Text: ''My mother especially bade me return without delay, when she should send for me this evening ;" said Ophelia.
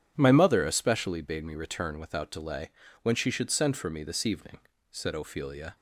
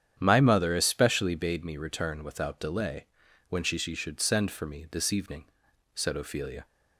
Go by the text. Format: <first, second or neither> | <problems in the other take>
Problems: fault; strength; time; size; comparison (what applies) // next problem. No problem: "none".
first | starts louder than the rest; strong; until 1.1 s; 9.5 dB; strong in the first // says "she" twice; at 3.7 s